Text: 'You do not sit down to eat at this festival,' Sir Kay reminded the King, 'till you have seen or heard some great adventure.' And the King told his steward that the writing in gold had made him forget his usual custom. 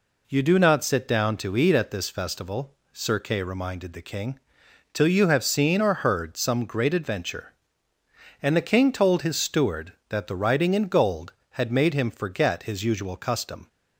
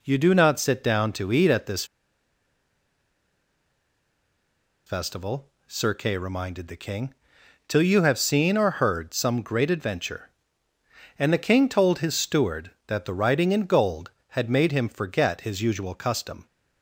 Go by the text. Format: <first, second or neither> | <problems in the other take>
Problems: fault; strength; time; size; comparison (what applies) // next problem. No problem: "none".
first | pauses between "this" and "festival"; strong; at 1.8 s; 3.0 s long